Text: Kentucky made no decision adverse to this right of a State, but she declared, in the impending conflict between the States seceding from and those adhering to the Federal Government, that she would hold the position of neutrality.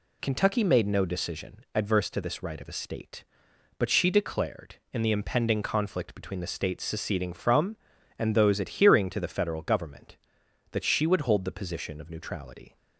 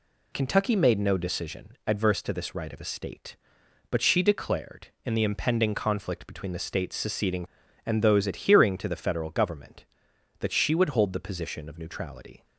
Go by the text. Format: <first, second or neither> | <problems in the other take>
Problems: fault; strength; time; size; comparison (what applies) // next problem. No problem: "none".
first | skips "from"; at 7.6 s